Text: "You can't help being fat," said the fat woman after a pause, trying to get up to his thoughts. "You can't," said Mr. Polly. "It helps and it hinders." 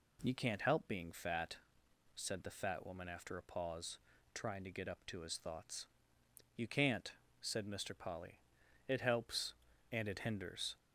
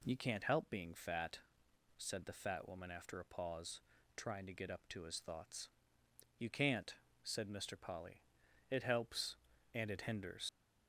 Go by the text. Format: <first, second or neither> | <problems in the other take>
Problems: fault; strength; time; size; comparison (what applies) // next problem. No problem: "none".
first | leaves "hinders" unfinished; at 10.4 s; 95 ms